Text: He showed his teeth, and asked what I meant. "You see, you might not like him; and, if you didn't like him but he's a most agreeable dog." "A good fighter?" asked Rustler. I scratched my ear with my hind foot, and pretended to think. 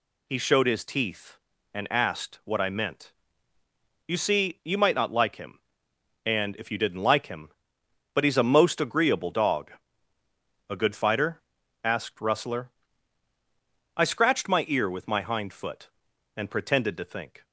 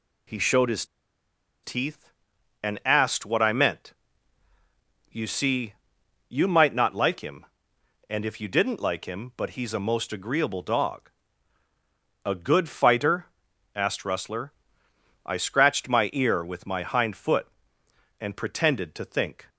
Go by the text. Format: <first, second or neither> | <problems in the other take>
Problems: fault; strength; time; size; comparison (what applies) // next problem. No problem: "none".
first | pauses between "his" and "teeth"; noticeable; at 0.8 s; 0.79 s long